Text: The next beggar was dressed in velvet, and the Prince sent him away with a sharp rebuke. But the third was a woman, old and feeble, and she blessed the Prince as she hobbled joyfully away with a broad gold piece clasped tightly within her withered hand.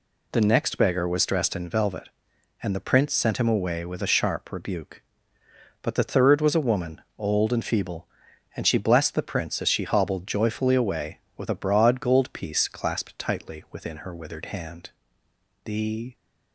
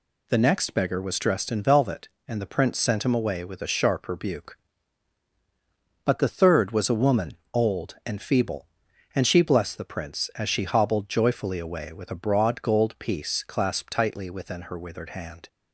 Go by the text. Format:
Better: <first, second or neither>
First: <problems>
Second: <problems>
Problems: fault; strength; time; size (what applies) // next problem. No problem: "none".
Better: second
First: goes on to say "The"; from 15.6 s on; 0.50 s long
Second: none